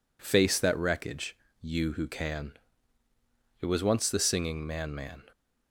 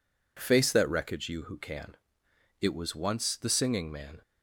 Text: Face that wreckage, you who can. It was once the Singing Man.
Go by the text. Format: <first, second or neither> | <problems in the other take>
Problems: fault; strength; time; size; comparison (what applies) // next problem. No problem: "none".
second | says "Man" twice; at 4.9 s